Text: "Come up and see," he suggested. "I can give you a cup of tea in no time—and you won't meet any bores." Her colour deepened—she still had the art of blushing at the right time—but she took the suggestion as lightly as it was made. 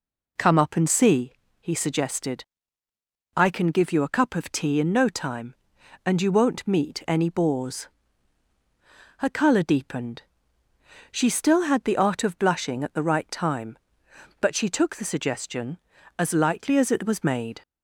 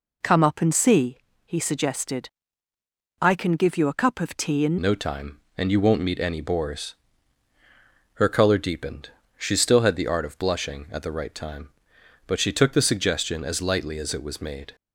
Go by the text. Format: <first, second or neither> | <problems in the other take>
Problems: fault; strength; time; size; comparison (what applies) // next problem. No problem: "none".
first | changes voice at "no"; from 4.8 s on; 9.9 s long